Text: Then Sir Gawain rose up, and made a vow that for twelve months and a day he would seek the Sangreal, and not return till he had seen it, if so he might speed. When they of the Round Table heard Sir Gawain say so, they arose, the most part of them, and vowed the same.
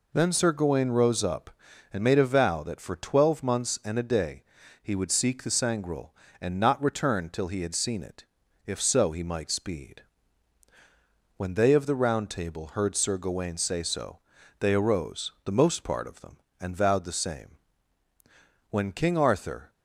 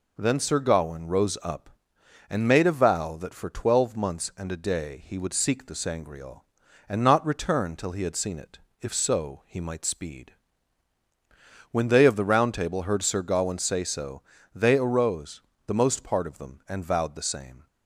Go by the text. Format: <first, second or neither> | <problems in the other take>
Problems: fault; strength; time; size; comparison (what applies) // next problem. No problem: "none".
second | pauses between "day" and "he"; at 4.4 s; 0.38 s long // goes on to say "When King Arthur"; noticeable; from 18.6 s on; 1.0 s long